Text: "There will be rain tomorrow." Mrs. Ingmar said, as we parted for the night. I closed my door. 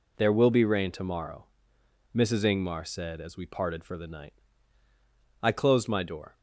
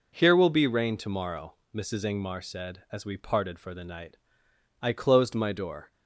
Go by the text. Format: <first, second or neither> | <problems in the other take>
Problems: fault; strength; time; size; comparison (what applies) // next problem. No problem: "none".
first | says "Here" for "There"; at 0.1 s